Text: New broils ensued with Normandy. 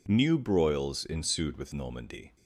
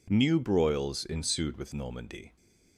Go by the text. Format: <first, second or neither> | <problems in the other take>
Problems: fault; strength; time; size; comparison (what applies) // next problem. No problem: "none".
neither | none